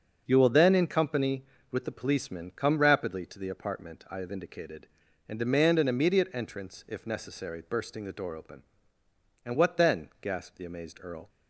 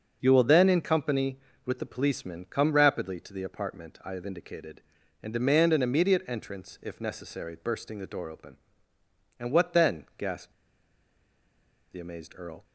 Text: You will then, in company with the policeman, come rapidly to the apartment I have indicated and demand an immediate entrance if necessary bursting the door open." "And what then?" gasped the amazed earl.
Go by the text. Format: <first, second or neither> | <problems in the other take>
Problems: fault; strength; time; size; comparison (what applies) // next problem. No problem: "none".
first | starts louder than the rest; noticeable; until 1.2 s; 6 dB; noticeable in the first // pauses between "gasped" and "the"; strong; at 10.5 s; 1.3 s long